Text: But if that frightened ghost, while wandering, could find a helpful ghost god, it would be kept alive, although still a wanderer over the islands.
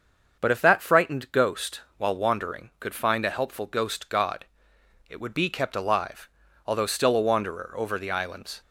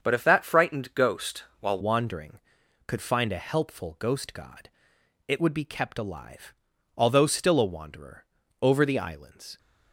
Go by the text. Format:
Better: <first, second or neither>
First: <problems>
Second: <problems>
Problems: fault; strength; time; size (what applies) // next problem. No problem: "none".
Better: first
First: starts louder than the rest; until 1.4 s; 6.5 dB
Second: starts louder than the rest; until 1.0 s; 7 dB // changes voice at "wandering"; from 1.8 s on; 7.7 s long // pauses between "wanderer" and "over"; at 8.2 s; 0.38 s long